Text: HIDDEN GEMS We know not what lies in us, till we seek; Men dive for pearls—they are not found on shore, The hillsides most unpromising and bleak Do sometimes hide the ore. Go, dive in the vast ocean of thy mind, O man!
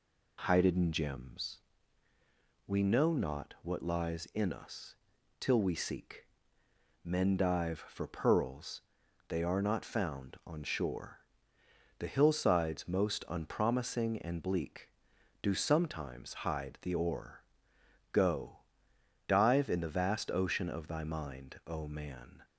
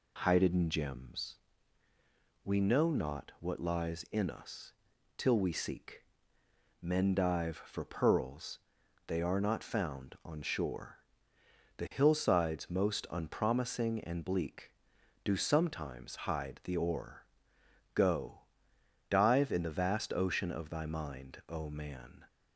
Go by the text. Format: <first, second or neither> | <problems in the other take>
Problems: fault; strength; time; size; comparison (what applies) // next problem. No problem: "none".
neither | pauses between "GEMS" and "We"; the same in both